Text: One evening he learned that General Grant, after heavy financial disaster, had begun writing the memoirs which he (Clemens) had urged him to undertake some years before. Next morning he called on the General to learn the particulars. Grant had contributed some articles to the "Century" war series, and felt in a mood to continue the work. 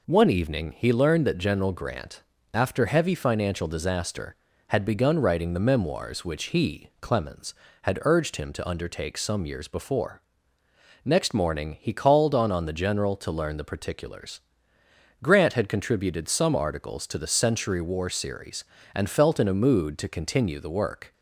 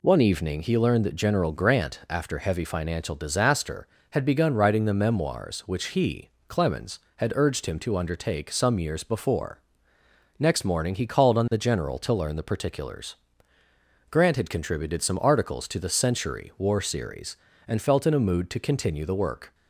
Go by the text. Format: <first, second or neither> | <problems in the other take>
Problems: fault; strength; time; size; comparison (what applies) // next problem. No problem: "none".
second | says "on" twice; at 12.5 s